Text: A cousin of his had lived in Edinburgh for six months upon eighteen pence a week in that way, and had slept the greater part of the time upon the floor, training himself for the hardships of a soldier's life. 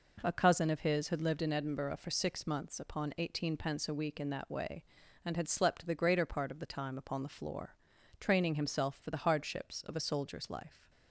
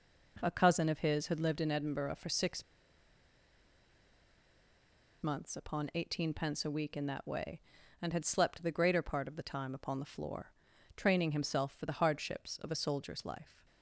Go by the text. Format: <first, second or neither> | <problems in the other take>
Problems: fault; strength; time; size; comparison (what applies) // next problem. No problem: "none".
first | pauses between "six" and "months"; strong; at 2.6 s; 2.5 s long